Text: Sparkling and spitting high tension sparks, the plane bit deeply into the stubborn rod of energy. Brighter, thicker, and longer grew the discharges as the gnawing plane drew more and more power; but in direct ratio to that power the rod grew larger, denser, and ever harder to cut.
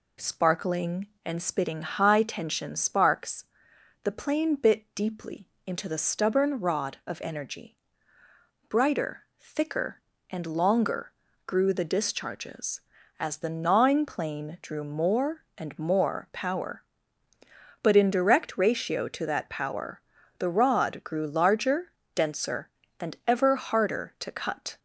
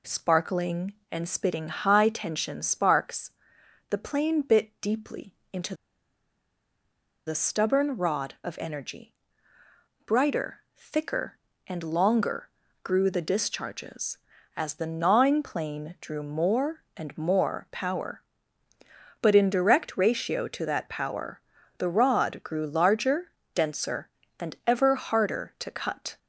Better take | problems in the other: first | pauses between "deeply" and "into"; slight; at 5.3 s; 0.18 s long; slight in the first // pauses between "into" and "the"; strong; at 5.7 s; 1.5 s long // pauses between "longer" and "grew"; slight; at 12.4 s; 0.34 s long; slight in the first // pauses between "power" and "the"; at 21.3 s; 0.38 s long; also in the first

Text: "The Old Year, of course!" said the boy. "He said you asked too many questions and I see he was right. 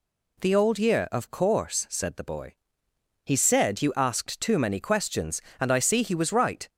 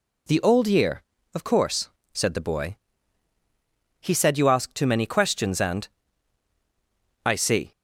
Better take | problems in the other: first | pauses between "and" and "I"; strong; at 5.8 s; 1.3 s long // stops before "he was right"; at 7.7 s

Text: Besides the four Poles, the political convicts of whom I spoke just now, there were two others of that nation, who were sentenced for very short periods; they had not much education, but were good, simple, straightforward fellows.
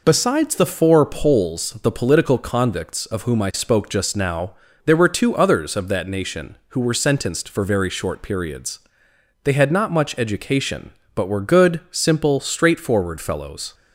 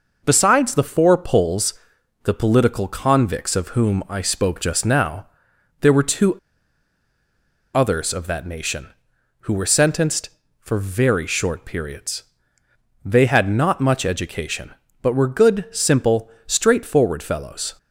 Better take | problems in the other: first | pauses between "two" and "others"; strong; at 6.3 s; 1.3 s long

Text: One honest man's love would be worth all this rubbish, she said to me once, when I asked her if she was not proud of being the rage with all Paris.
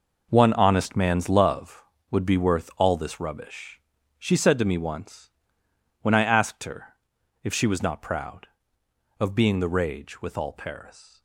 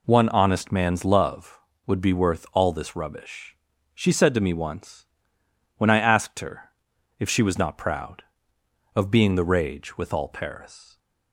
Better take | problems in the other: second | gets quieter; strong; throughout; 11.5 dB // pauses between "her" and "if"; noticeable; at 6.9 s; 0.50 s long; noticeable in the second

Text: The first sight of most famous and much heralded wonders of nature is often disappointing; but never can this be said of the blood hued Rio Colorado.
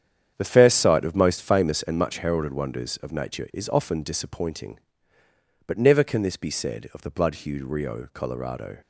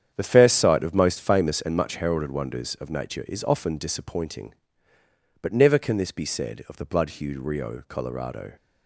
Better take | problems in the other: neither | starts louder than the rest; strong; the same in both

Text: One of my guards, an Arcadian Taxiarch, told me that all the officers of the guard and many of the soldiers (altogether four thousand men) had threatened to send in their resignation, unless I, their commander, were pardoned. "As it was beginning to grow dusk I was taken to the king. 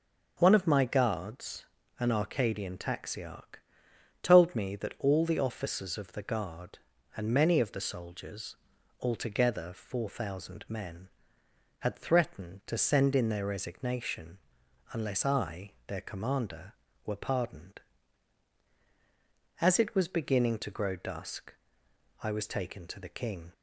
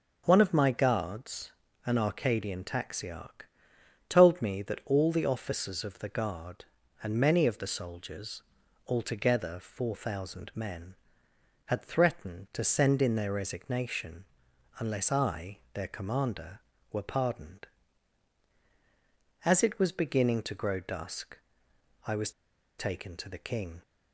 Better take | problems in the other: first | pauses between "dusk" and "I"; noticeable; at 21.3 s; 0.70 s long; noticeable in the first // pauses between "was" and "taken"; noticeable; at 22.3 s; 0.48 s long

